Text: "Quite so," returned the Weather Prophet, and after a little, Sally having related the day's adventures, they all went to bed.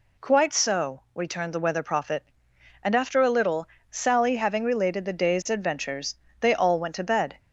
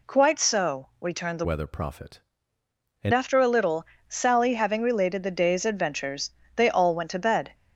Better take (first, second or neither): first